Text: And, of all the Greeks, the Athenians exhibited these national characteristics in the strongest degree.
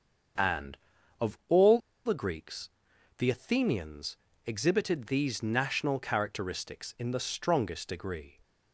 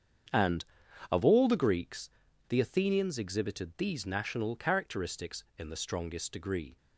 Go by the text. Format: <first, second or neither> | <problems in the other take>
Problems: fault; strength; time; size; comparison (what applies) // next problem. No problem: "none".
second | starts louder than the rest; until 2.1 s; 7 dB; strong in the second // pauses between "all" and "the"; slight; at 1.7 s; 0.26 s long // pauses between "Athenians" and "exhibited"; slight; at 4.1 s; 0.28 s long